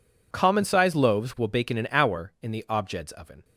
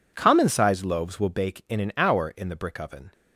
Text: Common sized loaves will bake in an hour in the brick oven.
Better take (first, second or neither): second